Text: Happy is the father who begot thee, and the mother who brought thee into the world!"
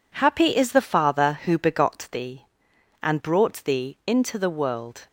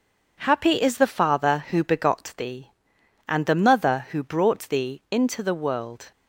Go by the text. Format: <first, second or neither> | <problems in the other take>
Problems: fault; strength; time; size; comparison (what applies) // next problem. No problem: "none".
second | skips "the mother who"; at 3.1 s